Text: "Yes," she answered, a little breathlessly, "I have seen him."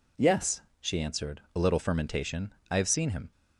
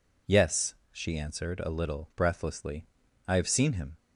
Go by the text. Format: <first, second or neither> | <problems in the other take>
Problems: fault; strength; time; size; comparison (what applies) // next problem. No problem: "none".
second | says "fermentation" for "breathlessly"; at 1.8 s